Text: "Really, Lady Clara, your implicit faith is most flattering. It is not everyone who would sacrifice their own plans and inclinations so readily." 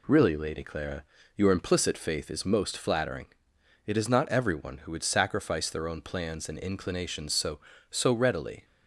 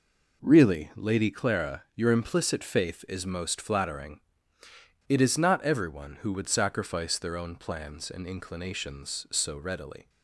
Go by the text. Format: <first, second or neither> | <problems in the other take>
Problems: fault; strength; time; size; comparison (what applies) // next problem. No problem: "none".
second | says "so" twice; at 7.8 s